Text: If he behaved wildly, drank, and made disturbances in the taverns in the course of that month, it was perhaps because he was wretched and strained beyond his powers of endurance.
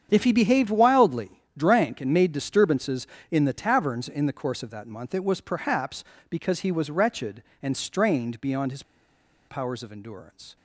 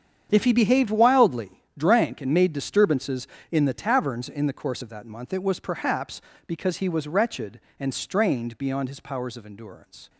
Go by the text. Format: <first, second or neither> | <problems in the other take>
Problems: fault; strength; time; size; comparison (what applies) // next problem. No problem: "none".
second | starts louder than the rest; strong; until 1.1 s; 8 dB; strong in the second // pauses between "his" and "powers"; noticeable; at 8.8 s; 0.65 s long